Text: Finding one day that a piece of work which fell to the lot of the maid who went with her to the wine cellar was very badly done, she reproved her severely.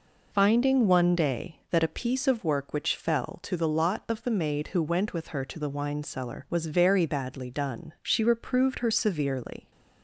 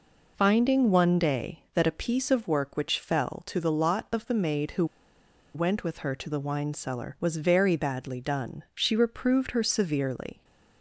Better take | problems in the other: first | pauses between "who" and "went"; noticeable; at 4.8 s; 0.69 s long

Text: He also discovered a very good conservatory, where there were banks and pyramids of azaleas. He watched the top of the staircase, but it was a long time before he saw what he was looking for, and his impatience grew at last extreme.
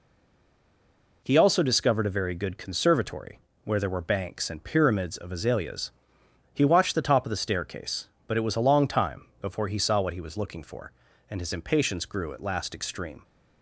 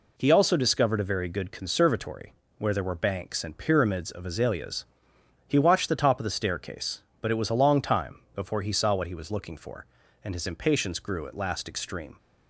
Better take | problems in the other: second | stays silent before the first word; noticeable; until 1.2 s; 1.2 s long // pauses between "time" and "before"; slight; at 9.2 s; 0.18 s long; slight in the second

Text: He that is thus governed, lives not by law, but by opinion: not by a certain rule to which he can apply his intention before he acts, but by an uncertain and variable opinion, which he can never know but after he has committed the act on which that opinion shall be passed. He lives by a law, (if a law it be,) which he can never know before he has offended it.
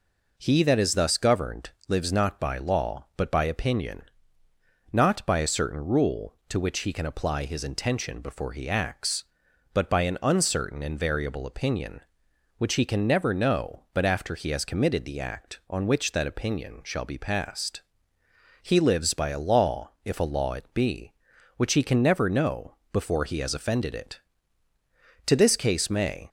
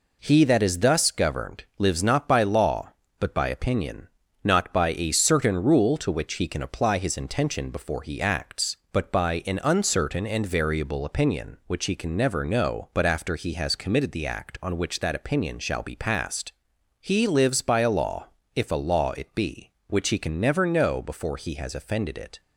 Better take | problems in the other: second | pauses between "know" and "before"; slight; at 22.7 s; 0.18 s long // goes on to say "To this case may"; noticeable; from 25.2 s on; 1.0 s long

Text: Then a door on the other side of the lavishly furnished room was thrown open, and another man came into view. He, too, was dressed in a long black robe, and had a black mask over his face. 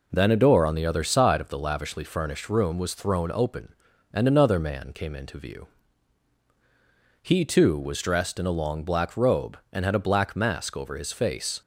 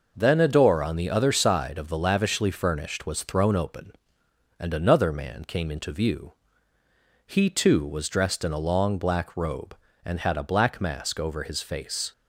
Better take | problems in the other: first | skips "room"; at 3.0 s

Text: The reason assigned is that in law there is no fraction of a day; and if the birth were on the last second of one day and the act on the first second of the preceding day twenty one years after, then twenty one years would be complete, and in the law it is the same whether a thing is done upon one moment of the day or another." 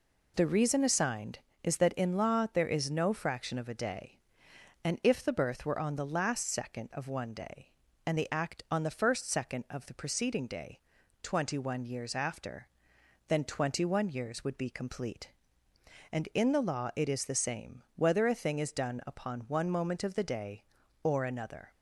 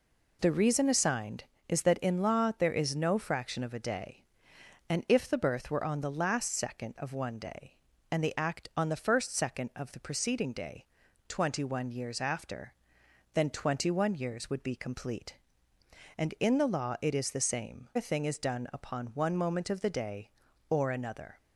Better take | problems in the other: first | pauses between "day" and "twenty"; at 10.8 s; 0.42 s long; also in the first // skips "whether"; at 17.9 s

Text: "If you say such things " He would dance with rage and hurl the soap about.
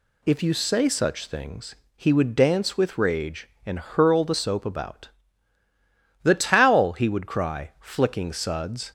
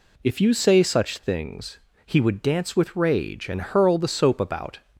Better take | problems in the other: second | goes on to say "The towel he would cry flicking suds"; strong; from 6.2 s on; 2.6 s long

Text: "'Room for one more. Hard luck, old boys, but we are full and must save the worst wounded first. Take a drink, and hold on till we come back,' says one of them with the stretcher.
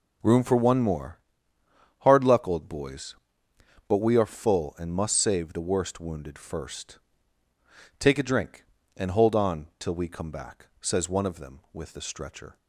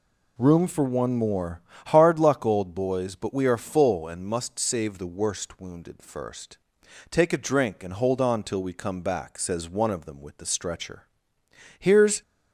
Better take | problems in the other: first | goes on to say "Here's"; slight; from 11.7 s on; 0.42 s long

